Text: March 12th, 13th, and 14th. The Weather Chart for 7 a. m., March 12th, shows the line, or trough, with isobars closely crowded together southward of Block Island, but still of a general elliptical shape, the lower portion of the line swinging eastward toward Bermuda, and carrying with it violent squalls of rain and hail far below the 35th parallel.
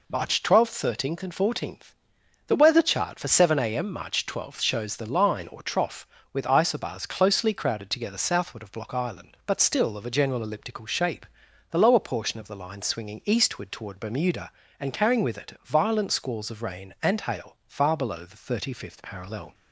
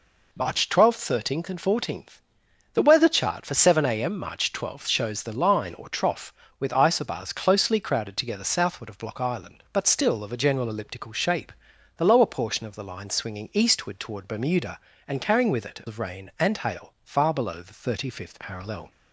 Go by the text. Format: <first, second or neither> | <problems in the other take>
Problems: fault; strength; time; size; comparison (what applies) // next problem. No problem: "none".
first | skips "violent squalls"; at 15.8 s